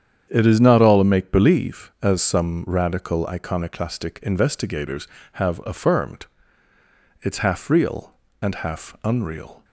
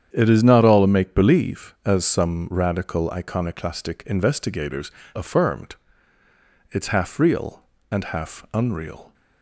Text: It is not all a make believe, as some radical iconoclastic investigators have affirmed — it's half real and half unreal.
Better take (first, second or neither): first